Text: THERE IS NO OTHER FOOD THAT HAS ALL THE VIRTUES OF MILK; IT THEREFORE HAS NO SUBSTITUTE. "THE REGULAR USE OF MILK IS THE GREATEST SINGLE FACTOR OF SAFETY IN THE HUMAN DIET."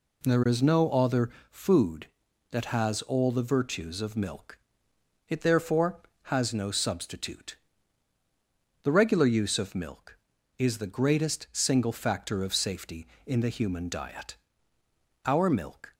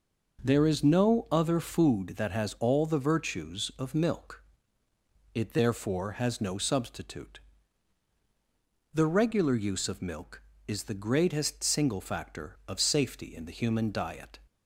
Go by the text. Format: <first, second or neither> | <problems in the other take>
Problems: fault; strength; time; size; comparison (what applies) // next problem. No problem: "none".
second | pauses between "OTHER" and "FOOD"; slight; at 1.2 s; 0.20 s long // goes on to say "OUR MILK"; noticeable; from 15.2 s on; 0.68 s long